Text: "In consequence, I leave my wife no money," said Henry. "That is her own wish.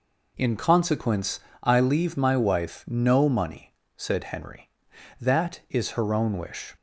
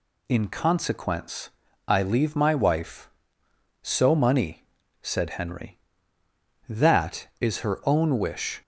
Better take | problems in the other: first | says "so" for "no"; at 3.8 s

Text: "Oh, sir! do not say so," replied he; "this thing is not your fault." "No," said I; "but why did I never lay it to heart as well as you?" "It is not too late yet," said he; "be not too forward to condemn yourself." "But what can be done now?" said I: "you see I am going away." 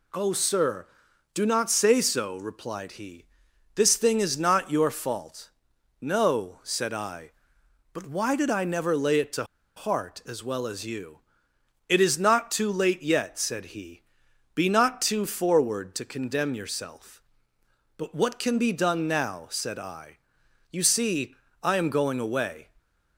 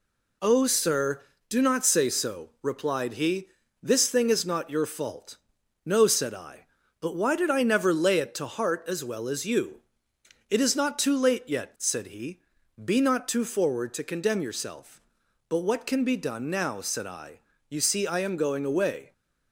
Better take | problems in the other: second | pauses between "to" and "heart"; slight; at 9.4 s; 0.32 s long // pauses between "see" and "I"; slight; at 21.3 s; 0.26 s long

